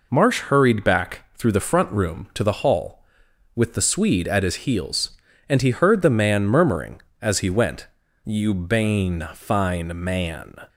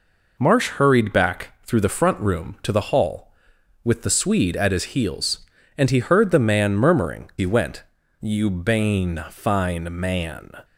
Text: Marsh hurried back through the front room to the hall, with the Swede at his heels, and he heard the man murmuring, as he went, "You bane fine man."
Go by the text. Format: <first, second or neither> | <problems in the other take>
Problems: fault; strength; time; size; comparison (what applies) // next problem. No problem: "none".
first | skips "as"; at 7.3 s